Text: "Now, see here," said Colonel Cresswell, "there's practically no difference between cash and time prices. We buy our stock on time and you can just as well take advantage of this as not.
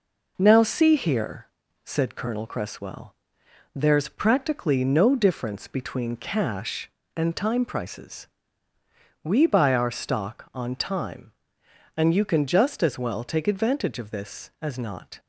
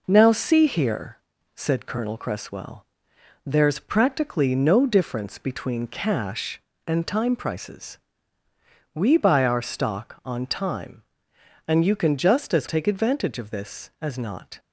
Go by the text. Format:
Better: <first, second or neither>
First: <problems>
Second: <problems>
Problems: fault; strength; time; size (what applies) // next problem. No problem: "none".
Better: first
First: none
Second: skips "well"; at 12.6 s